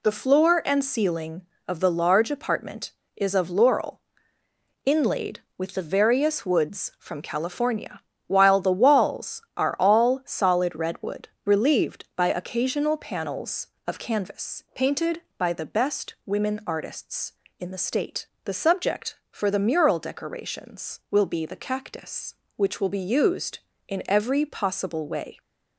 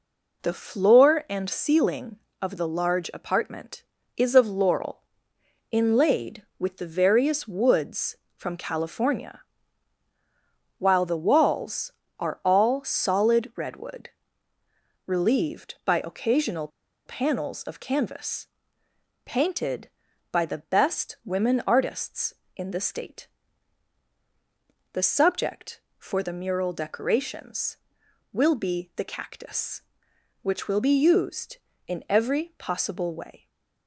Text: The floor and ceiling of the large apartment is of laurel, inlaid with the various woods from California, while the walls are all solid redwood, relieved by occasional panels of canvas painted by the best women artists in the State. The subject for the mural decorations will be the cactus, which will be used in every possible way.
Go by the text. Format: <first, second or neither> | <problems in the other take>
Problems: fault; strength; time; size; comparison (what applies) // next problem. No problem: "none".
first | pauses between "occasional" and "panels"; at 16.6 s; 0.37 s long // pauses between "canvas" and "painted"; noticeable; at 18.4 s; 0.76 s long // stays silent after the last word; slight; from 33.3 s on; 0.5 s long